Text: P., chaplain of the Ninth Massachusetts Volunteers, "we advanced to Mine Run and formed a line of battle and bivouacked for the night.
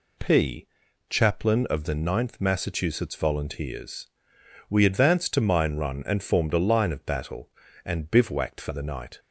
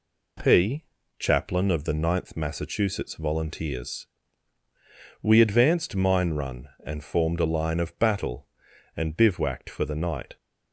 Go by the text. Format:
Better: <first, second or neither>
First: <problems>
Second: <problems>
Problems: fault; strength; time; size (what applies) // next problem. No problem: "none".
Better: first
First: none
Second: skips "to"; at 5.9 s